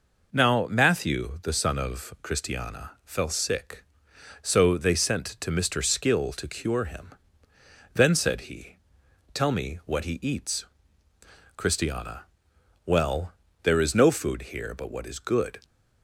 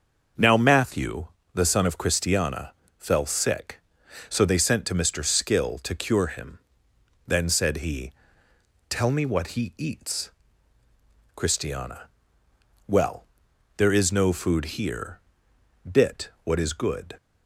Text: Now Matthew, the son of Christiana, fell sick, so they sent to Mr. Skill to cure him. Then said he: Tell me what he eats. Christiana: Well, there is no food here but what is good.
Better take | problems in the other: first | starts louder than the rest; noticeable; until 1.6 s; 6 dB // says "bit" for "but"; at 15.8 s

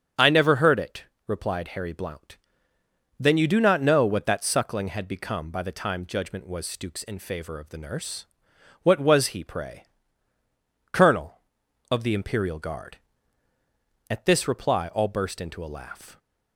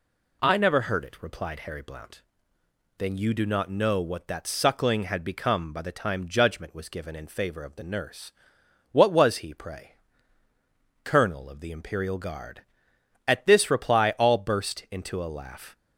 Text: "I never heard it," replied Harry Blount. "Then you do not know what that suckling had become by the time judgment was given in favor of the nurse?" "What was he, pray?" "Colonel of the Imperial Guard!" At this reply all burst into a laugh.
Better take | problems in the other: second | starts louder than the rest; strong; until 1.4 s; 8 dB // says "stooks" for "given"; at 6.6 s

